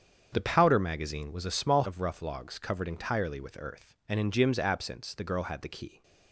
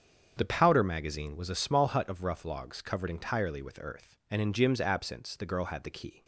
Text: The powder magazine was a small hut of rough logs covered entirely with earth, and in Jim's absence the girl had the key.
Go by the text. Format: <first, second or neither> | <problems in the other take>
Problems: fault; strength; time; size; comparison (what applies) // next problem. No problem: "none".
second | starts louder than the rest; strong; until 1.3 s; 7.5 dB; strong in the second // skips "hut"; at 1.8 s